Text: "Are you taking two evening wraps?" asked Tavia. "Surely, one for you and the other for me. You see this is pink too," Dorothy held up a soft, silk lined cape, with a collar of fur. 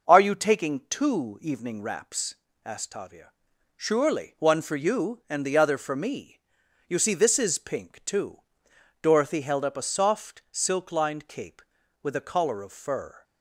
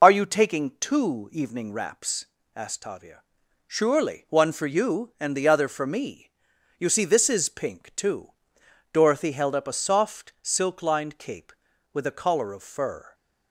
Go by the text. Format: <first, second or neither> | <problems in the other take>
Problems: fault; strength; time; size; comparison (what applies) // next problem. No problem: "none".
first | loses the start of "Are"; at 0.0 s; 40 ms